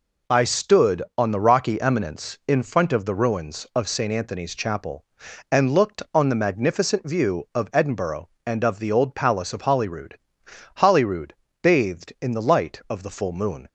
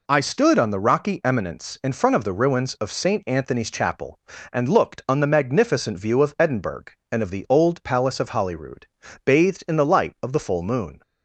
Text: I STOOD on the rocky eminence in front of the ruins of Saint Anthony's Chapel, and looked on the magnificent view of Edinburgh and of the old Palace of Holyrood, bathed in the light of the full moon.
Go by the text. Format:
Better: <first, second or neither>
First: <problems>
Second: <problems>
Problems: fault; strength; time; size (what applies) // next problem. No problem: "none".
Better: second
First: says "Holyrood" twice; at 10.7 s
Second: none